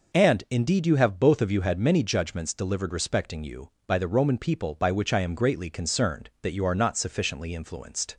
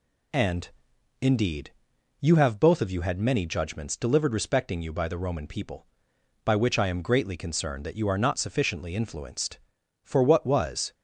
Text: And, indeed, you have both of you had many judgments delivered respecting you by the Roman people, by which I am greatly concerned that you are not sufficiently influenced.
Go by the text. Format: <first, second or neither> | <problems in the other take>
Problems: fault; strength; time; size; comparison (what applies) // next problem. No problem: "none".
first | goes on to say "For what was"; noticeable; from 10.0 s on; 0.90 s long